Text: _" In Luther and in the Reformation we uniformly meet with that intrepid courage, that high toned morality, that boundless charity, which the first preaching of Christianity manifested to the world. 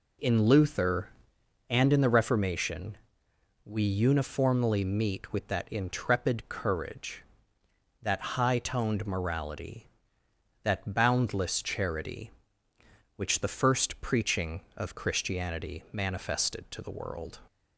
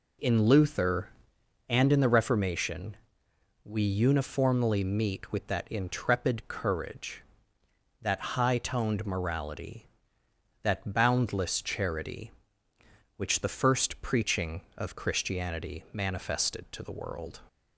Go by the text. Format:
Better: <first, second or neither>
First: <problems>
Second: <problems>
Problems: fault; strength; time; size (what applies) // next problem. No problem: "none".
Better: neither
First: pauses between "Reformation" and "we"; noticeable; at 2.9 s; 0.66 s long // pauses between "that" and "high"; slight; at 8.1 s; 0.16 s long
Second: pauses between "Reformation" and "we"; noticeable; at 2.9 s; 0.66 s long // pauses between "that" and "high"; slight; at 8.1 s; 0.16 s long